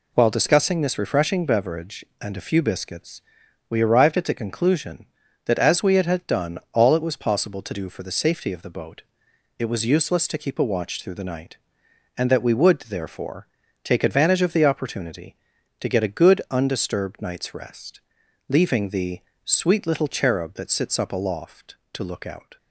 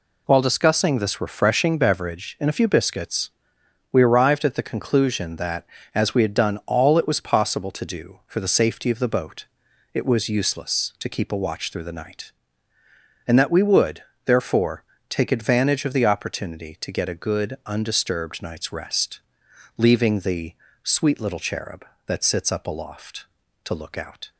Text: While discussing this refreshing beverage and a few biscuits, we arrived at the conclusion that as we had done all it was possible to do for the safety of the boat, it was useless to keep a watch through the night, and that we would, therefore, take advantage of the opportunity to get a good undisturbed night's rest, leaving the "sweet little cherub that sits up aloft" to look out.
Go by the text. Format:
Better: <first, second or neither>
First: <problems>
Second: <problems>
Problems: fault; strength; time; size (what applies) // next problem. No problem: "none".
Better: second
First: says "had" twice; at 6.0 s // pauses between "the" and "sweet"; slight; at 19.2 s; 0.24 s long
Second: pauses between "the" and "sweet"; slight; at 20.5 s; 0.30 s long